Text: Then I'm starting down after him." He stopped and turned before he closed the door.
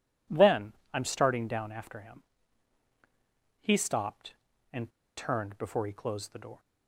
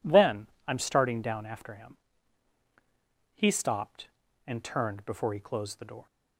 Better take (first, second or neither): second